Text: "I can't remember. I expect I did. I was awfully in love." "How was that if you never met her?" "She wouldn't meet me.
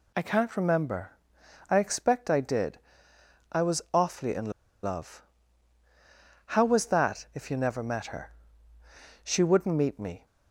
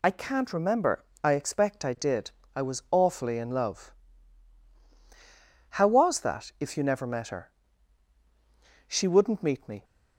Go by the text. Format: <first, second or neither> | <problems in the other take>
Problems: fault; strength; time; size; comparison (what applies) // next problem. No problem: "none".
second | pauses between "in" and "love"; slight; at 4.5 s; 0.31 s long